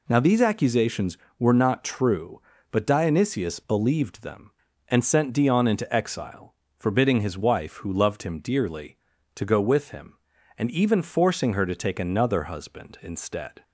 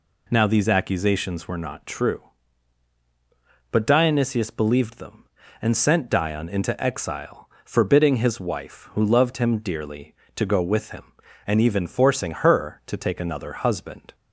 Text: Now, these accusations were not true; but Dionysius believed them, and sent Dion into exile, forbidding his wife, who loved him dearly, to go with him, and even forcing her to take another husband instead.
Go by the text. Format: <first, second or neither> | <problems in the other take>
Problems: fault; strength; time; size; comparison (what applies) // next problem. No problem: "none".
first | stops before "instead"; at 14.1 s